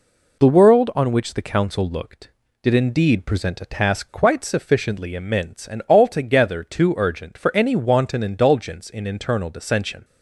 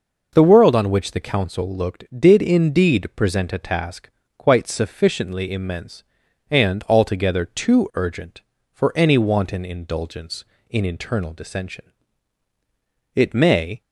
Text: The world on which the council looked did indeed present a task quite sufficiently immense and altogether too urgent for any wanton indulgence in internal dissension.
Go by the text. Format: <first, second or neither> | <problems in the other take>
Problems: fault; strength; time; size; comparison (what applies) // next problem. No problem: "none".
first | pauses between "task" and "quite"; slight; at 4.0 s; 0.26 s long // goes on to say "It may"; noticeable; from 13.1 s on; 0.66 s long